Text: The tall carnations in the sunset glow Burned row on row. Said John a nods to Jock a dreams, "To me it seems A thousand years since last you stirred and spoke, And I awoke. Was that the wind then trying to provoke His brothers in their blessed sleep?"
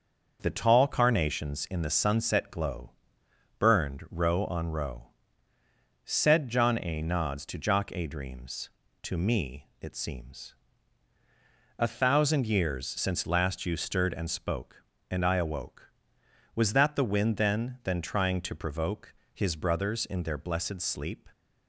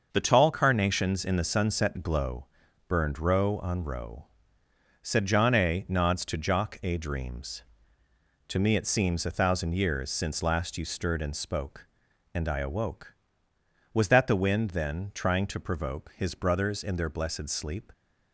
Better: second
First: starts louder than the rest; until 1.4 s; 6.5 dB // pauses between "glow" and "Burned"; noticeable; at 2.9 s; 0.66 s long // pauses between "seems" and "A"; at 10.5 s; 1.2 s long // says "then" twice; at 17.8 s // pauses between "provoke" and "His"; slight; at 19.1 s; 0.22 s long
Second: starts louder than the rest; until 1.1 s; 6.5 dB // pauses between "glow" and "Burned"; at 2.4 s; 0.42 s long

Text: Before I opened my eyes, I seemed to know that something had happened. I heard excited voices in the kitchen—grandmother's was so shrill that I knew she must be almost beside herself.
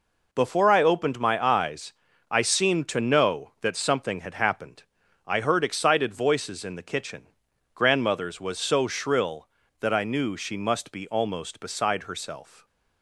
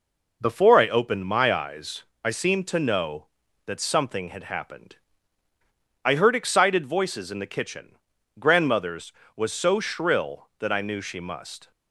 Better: first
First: none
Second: stops before "be almost beside herself"; at 11.7 s

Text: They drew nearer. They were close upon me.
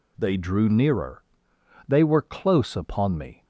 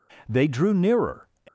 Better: first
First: none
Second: stops before "They were close upon me"; at 1.4 s

